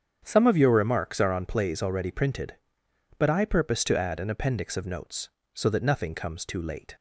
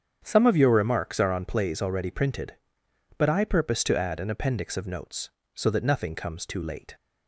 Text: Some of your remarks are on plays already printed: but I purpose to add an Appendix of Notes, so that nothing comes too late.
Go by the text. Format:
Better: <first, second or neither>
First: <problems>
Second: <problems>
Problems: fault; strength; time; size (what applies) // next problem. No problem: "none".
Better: neither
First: starts louder than the rest; strong; until 1.2 s; 8 dB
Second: starts louder than the rest; strong; until 1.2 s; 8 dB